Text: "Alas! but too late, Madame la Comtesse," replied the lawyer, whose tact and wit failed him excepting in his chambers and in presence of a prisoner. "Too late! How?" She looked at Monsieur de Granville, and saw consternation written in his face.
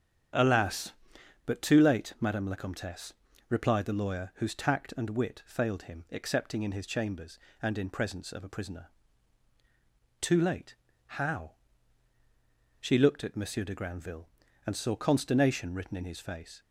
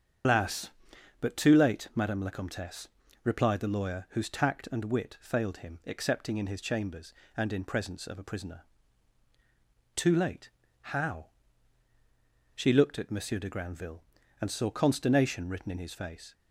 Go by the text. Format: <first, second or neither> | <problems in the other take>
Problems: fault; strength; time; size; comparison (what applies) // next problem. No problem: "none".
first | loses the start of "Alas"; at 0.2 s; 145 ms // starts louder than the rest; strong; until 1.7 s; 7.5 dB; strong in the first